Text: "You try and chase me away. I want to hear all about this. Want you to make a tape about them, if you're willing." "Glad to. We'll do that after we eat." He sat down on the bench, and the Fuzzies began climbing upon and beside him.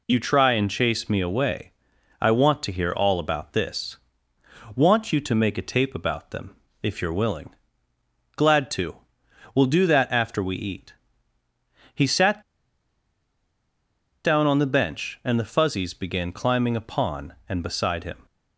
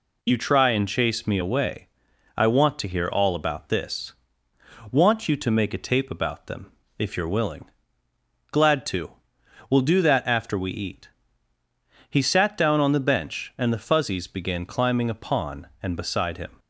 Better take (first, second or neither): second